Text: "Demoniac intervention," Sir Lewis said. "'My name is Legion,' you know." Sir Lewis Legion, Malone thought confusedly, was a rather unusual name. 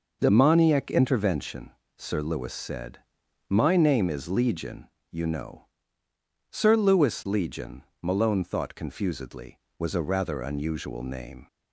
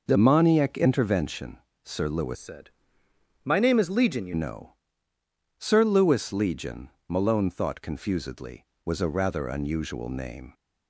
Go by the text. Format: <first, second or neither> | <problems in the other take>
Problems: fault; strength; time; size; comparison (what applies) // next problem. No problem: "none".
first | changes voice from "said" to "you"; from 2.3 to 4.3 s; 2.0 s long